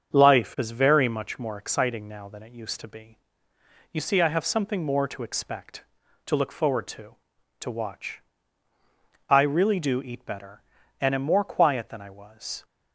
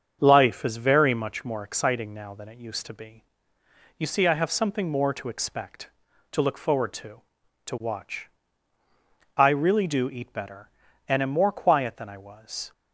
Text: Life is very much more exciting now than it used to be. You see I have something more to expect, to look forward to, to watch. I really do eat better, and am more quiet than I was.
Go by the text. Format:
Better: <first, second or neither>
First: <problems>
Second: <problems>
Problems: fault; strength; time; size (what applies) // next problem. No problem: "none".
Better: neither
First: starts louder than the rest; until 1.1 s; 7 dB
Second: starts louder than the rest; until 1.2 s; 7 dB